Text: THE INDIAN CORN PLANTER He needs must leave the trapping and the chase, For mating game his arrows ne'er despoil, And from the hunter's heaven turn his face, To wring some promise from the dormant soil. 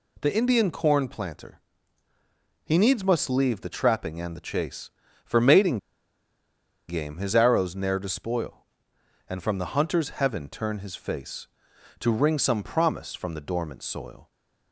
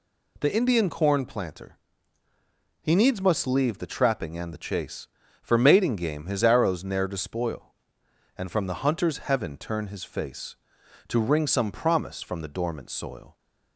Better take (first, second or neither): second